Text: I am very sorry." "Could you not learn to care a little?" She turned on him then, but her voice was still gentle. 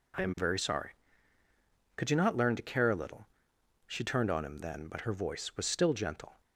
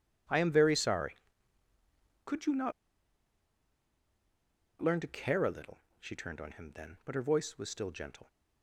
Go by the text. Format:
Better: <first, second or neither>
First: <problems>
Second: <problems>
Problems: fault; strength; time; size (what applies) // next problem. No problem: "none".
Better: first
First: none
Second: pauses between "not" and "learn"; strong; at 2.7 s; 2.0 s long